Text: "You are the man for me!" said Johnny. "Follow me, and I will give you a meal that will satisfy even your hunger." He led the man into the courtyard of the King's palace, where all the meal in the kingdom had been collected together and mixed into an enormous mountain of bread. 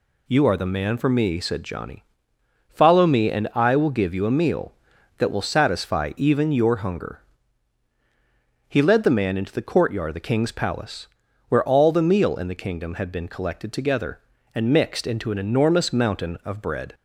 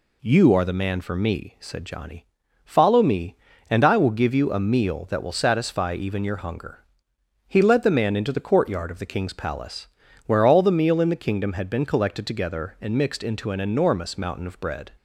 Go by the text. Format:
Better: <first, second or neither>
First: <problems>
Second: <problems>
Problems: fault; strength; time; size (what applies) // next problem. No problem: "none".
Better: neither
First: none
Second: none